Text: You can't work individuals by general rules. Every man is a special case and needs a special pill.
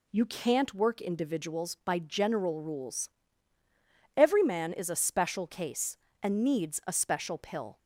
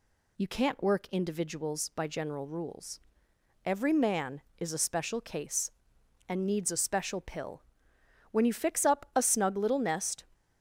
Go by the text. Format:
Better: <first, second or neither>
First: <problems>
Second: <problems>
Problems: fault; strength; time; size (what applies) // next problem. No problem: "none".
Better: first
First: none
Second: goes on to say "When you fix up a snug little nest"; strong; from 8.3 s on; 1.9 s long